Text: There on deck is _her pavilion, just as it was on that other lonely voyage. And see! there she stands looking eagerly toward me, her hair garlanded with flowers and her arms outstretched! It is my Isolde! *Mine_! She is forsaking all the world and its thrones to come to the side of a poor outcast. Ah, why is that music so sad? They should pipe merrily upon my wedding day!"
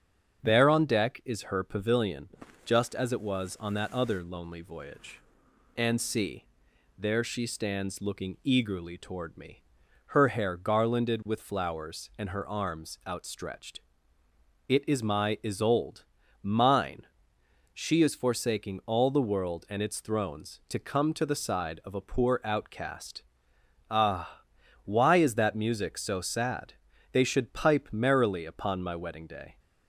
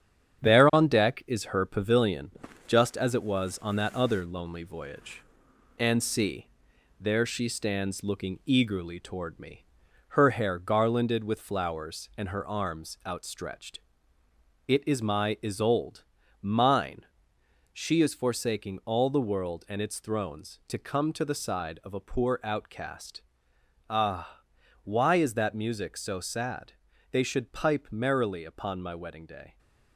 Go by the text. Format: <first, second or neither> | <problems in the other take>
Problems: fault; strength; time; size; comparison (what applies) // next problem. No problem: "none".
first | gets quieter; noticeable; throughout; 6 dB // starts louder than the rest; strong; until 1.5 s; 9 dB; strong in the first